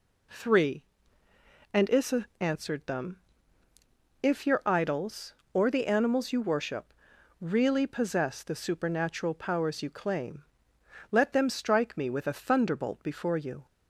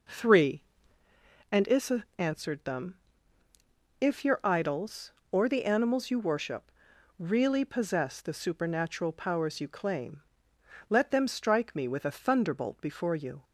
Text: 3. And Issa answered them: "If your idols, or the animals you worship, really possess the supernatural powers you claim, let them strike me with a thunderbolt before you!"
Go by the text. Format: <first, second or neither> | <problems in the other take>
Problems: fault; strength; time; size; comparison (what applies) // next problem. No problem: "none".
first | starts louder than the rest; noticeable; until 1.0 s; 5 dB